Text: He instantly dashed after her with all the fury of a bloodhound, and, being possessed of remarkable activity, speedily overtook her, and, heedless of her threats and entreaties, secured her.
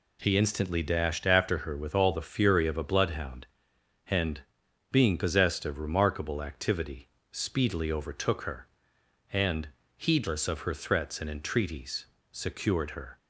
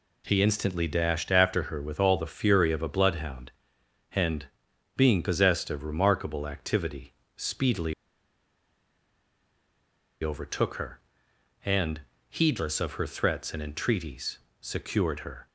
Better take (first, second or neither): first